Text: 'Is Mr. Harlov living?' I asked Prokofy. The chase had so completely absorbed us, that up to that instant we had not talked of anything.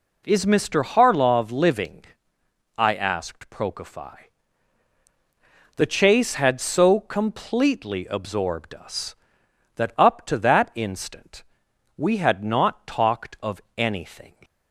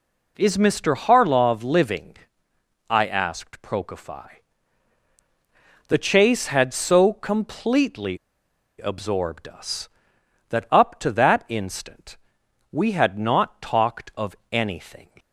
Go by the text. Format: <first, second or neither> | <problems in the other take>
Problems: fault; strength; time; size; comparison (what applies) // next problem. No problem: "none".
first | pauses between "completely" and "absorbed"; noticeable; at 8.1 s; 0.61 s long // pauses between "instant" and "we"; noticeable; at 12.1 s; 0.54 s long; noticeable in the first // pauses between "of" and "anything"; slight; at 14.3 s; 0.16 s long; slight in the first